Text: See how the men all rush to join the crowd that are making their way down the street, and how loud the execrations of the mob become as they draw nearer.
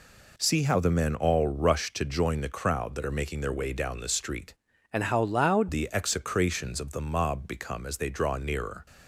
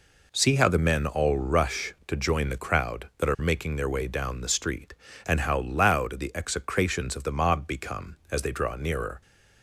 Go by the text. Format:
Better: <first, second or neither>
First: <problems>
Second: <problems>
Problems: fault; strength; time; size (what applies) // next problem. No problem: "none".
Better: second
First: changes voice from "and" to "loud"; from 4.9 to 5.6 s; 0.7 s long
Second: none